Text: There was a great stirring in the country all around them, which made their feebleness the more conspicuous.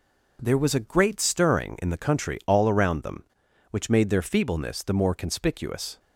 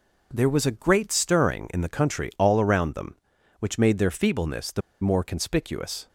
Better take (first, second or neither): first